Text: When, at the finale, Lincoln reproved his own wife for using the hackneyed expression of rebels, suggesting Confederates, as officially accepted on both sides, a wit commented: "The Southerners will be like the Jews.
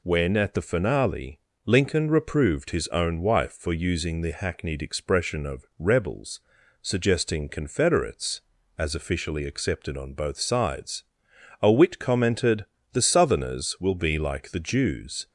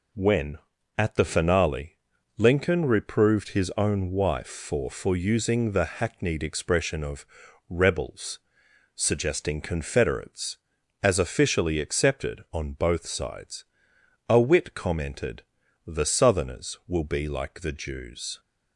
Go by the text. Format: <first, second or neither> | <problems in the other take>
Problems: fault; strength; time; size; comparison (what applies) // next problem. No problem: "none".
first | says "for" twice; at 4.8 s // pauses between "of" and "rebels"; at 7.2 s; 0.42 s long